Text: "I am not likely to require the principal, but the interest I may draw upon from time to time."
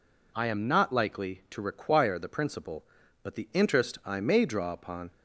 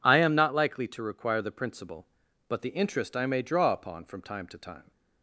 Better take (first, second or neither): second